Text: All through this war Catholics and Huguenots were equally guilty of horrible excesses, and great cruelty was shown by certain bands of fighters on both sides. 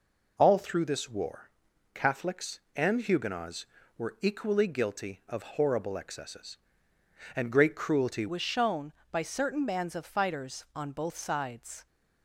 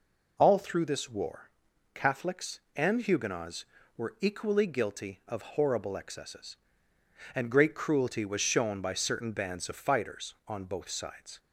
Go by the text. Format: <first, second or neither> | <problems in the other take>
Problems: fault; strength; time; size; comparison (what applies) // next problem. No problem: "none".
second | pauses between "war" and "Catholics"; noticeable; at 1.4 s; 0.46 s long; noticeable in the second // changes voice at "was"; from 8.2 s on; 3.6 s long